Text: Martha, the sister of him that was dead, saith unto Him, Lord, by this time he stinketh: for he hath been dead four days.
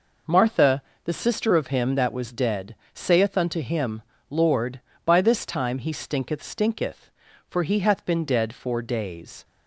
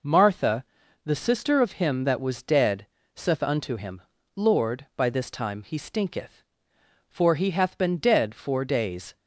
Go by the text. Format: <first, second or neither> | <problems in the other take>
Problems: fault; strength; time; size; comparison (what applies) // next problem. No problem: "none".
second | says "stinketh" twice; at 6.4 s